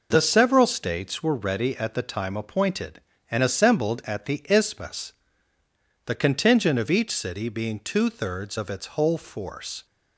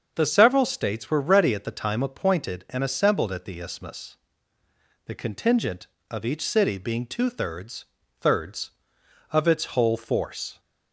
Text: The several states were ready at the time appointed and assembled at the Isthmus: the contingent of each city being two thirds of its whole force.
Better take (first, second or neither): first